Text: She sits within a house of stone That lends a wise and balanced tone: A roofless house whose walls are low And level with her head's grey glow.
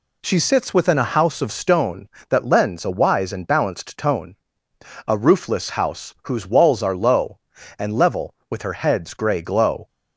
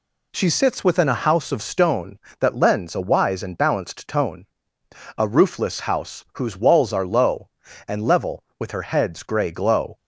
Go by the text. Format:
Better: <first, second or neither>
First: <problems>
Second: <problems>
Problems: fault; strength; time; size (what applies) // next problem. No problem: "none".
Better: neither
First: none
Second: none